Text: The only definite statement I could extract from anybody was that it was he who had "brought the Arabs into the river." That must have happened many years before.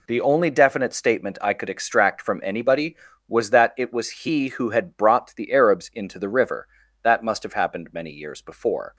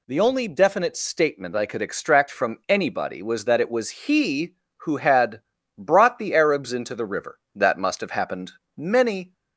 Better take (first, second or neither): first